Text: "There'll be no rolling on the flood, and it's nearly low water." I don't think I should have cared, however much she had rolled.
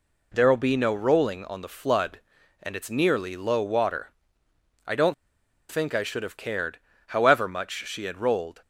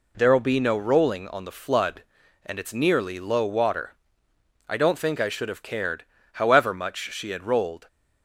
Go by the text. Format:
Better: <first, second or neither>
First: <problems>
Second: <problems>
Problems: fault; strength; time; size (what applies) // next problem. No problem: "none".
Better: second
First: pauses between "don't" and "think"; noticeable; at 5.1 s; 0.55 s long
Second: none